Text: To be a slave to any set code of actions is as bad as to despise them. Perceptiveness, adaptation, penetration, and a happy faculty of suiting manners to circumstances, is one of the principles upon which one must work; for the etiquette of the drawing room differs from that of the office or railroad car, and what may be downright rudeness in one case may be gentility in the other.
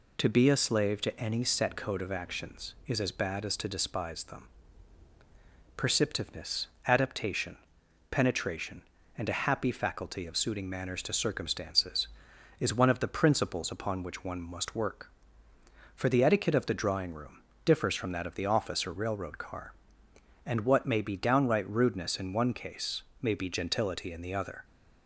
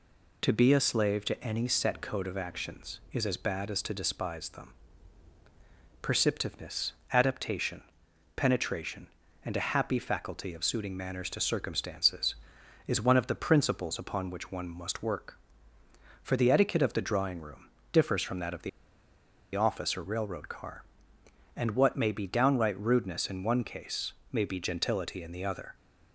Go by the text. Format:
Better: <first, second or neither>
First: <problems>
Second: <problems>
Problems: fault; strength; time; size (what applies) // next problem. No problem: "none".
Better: first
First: pauses between "room" and "differs"; slight; at 17.4 s; 0.24 s long // pauses between "case" and "may"; slight; at 23.0 s; 0.18 s long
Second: pauses between "room" and "differs"; slight; at 17.6 s; 0.24 s long // pauses between "the" and "office"; noticeable; at 18.6 s; 0.85 s long // pauses between "case" and "may"; slight; at 24.1 s; 0.18 s long